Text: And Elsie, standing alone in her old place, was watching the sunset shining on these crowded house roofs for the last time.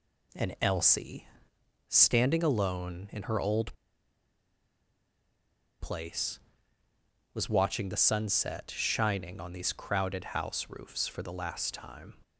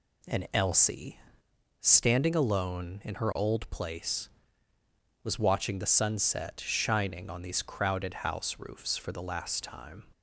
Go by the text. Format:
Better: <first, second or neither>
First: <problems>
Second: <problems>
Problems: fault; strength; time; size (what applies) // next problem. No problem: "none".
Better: second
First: pauses between "old" and "place"; strong; at 3.7 s; 2.0 s long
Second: none